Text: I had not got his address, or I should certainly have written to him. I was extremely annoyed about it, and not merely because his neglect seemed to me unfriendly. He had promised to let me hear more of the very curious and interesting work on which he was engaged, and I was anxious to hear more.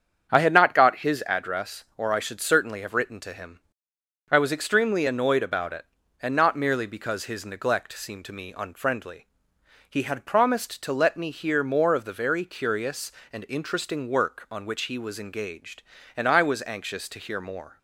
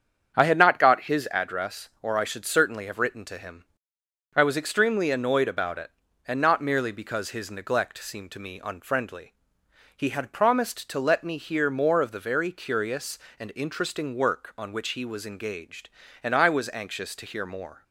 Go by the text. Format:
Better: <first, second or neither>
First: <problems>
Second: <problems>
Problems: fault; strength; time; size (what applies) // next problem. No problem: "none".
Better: neither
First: starts louder than the rest; strong; until 1.3 s; 7.5 dB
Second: starts louder than the rest; strong; until 1.3 s; 7.5 dB